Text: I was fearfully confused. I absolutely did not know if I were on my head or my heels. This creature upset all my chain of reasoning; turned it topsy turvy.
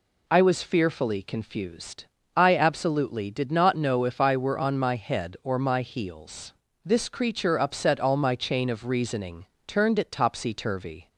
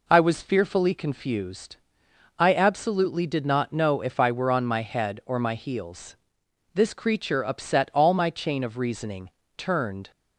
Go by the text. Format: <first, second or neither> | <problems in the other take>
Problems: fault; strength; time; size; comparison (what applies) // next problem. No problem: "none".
first | stops before "it topsy turvy"; at 10.1 s